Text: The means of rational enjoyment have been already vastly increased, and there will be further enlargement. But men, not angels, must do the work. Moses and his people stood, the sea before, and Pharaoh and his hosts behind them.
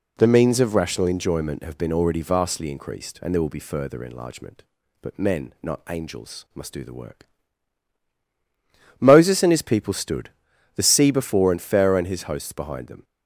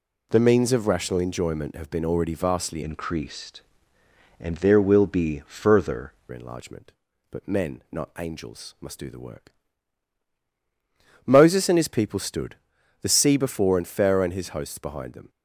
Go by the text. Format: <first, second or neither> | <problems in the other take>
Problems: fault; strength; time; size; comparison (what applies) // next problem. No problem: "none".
first | changes voice from "increased" to "further"; from 2.8 to 6.1 s; 3.3 s long